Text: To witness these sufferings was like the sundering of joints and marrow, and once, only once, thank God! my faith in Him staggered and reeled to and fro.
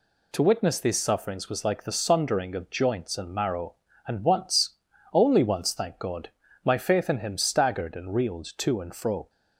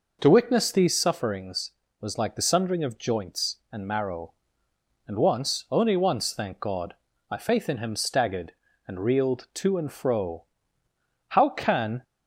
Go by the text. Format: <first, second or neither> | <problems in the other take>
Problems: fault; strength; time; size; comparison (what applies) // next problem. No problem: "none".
first | goes on to say "How can"; noticeable; from 11.2 s on; 0.74 s long